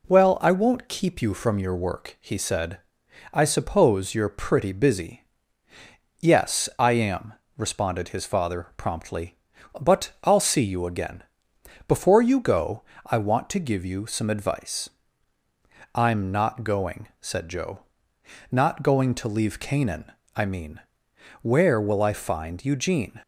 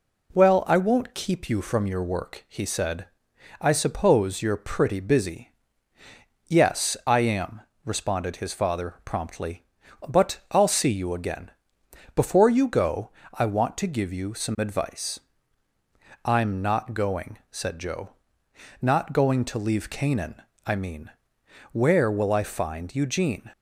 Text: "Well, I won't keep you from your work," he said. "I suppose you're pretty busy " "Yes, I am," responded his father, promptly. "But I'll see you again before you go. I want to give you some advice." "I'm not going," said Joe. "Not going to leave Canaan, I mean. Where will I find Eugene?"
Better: neither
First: pauses between "again" and "before"; noticeable; at 11.2 s; 0.64 s long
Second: pauses between "again" and "before"; noticeable; at 11.5 s; 0.64 s long

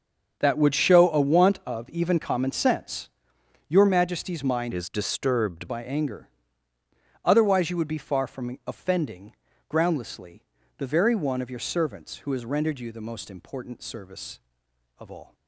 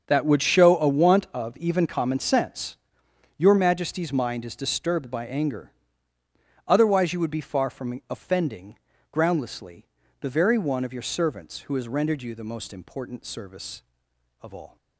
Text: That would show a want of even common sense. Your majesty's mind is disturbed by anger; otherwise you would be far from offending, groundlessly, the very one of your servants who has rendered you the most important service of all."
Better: second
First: starts louder than the rest; until 1.4 s; 7 dB // changes voice from "is" to "disturbed"; from 4.7 to 5.6 s; 0.9 s long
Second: starts louder than the rest; until 1.0 s; 6.5 dB

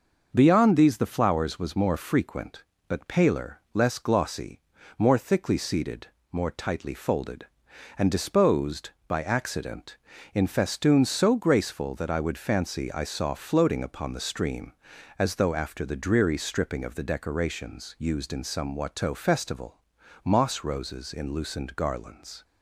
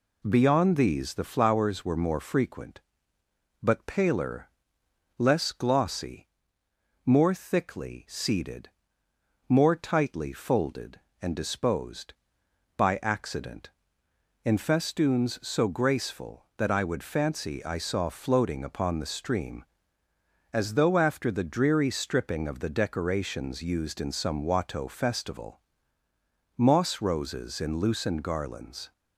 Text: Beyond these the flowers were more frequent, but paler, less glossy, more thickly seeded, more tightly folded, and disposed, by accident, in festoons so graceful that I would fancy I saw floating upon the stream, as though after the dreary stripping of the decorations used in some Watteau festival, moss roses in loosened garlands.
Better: second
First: says "was" for "were"; at 1.5 s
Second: none

